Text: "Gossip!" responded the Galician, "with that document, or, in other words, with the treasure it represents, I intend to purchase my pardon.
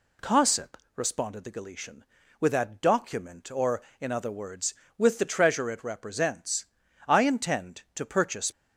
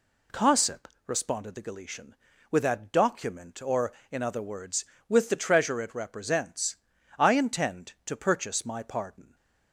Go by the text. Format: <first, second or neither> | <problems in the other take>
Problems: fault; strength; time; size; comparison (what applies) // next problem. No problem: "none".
second | stops before "my pardon"; at 8.5 s